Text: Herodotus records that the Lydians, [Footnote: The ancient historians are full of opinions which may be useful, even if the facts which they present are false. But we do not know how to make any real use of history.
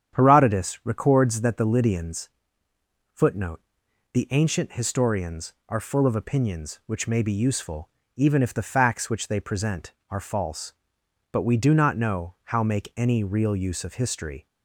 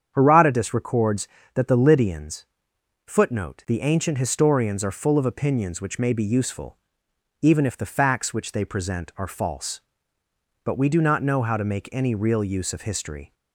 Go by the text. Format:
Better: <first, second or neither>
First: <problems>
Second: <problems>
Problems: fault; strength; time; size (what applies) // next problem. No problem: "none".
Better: second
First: starts louder than the rest; strong; until 1.2 s; 9 dB // skips "to"; at 12.6 s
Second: starts louder than the rest; strong; until 1.1 s; 8 dB